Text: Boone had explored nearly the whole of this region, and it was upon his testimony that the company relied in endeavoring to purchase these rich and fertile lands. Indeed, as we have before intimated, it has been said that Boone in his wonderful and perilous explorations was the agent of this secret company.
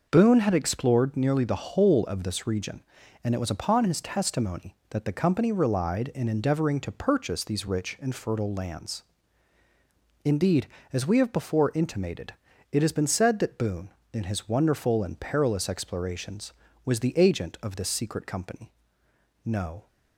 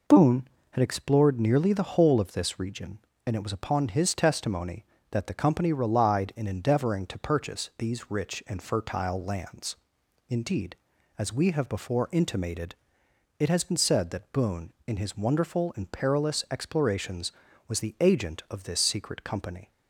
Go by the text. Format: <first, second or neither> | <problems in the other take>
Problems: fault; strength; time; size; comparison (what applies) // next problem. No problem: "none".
second | goes on to say "No"; slight; from 19.4 s on; 0.42 s long